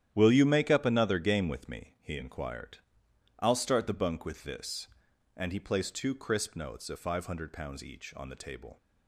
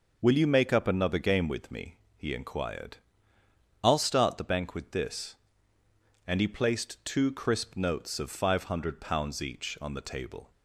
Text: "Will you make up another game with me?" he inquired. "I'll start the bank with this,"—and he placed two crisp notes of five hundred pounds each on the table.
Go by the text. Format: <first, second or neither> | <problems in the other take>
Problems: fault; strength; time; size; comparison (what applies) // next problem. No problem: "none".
second | starts louder than the rest; strong; until 1.1 s; 11 dB // says "bunk" for "bank"; at 3.9 s